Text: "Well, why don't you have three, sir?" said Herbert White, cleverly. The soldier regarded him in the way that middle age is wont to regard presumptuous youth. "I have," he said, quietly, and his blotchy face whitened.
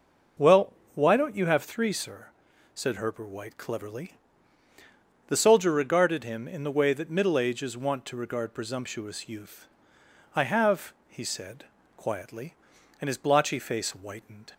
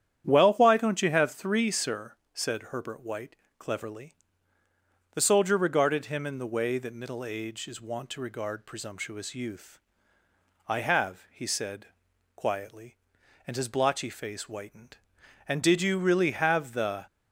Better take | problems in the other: first | starts louder than the rest; strong; until 1.2 s; 9.5 dB // goes on to say "And did you really have the"; from 15.4 s on; 1.5 s long

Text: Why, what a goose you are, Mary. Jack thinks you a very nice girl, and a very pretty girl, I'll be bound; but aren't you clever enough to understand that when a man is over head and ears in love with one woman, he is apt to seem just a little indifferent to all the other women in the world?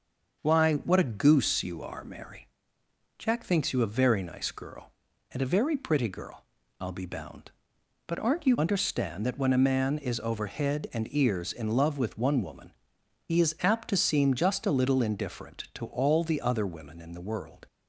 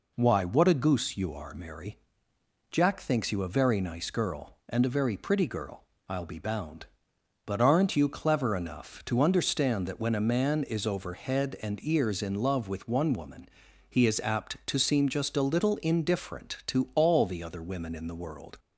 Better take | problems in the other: second | starts louder than the rest; until 1.4 s; 6.5 dB // skips "clever enough to"; at 8.5 s

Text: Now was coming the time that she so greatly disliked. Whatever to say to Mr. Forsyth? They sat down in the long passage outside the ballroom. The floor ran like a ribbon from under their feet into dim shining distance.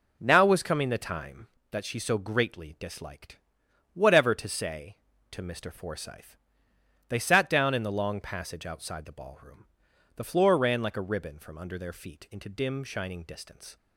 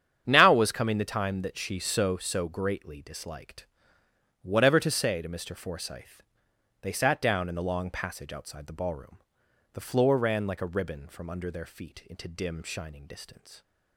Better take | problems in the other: first | starts louder than the rest; strong; until 1.2 s; 8.5 dB // says "so" twice; at 2.1 s

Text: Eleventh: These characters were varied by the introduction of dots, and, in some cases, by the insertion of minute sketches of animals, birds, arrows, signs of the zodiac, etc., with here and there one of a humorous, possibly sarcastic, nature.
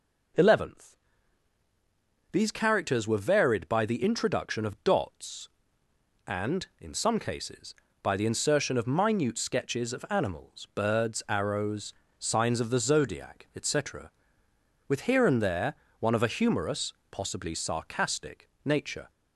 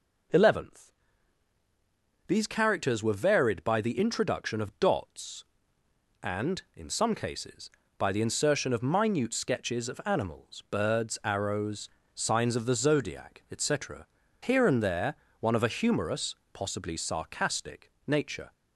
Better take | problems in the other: first | skips "with"; at 14.2 s // pauses between "there" and "one"; slight; at 15.1 s; 0.26 s long; slight in the first

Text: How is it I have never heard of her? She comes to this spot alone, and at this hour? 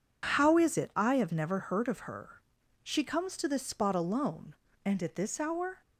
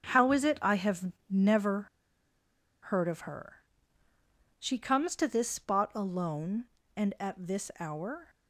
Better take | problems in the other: first | starts louder than the rest; strong; until 1.0 s; 7 dB // pauses between "have" and "never"; slight; at 1.1 s; 0.18 s long // pauses between "never" and "heard"; at 1.8 s; 1.0 s long

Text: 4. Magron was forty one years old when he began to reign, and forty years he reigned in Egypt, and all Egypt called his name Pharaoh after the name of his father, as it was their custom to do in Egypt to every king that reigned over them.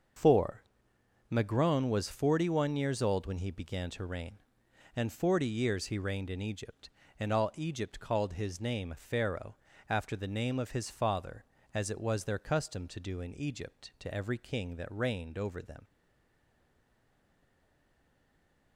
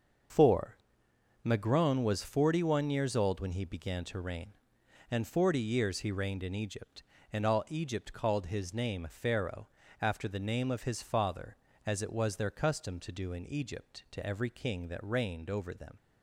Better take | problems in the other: second | starts louder than the rest; until 1.9 s; 6.5 dB; also in the second // pauses between "Pharaoh" and "after"; slight; at 9.5 s; 0.34 s long; slight in the second // stays silent after the last word; strong; from 15.8 s on; 2.9 s long

